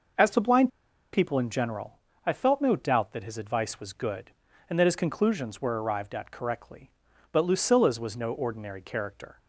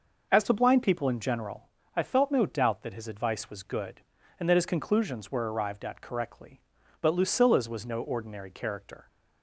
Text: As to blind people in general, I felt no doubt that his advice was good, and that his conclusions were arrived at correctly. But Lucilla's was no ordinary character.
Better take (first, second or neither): second